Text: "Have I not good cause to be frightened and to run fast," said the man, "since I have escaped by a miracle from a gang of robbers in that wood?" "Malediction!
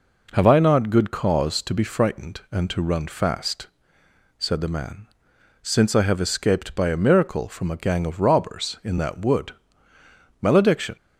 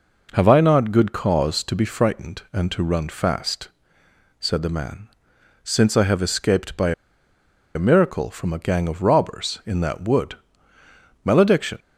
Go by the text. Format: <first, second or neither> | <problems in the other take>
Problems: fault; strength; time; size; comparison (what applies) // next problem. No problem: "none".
first | pauses between "by" and "a"; noticeable; at 6.9 s; 0.83 s long